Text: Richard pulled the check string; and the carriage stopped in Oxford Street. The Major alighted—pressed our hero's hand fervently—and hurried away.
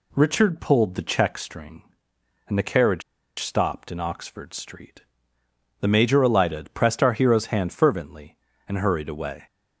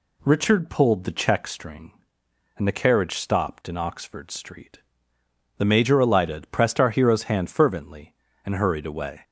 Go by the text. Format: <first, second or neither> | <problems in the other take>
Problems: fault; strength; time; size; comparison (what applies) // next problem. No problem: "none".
second | pauses between "carriage" and "stopped"; at 3.0 s; 0.37 s long